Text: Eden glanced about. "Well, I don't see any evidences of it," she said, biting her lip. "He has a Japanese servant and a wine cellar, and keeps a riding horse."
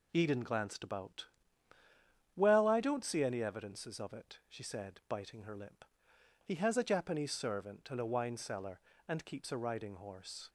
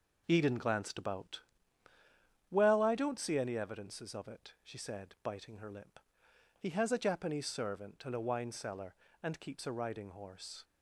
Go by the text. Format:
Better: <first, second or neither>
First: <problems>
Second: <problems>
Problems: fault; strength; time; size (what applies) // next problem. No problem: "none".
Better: first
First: none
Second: starts louder than the rest; noticeable; until 1.5 s; 5 dB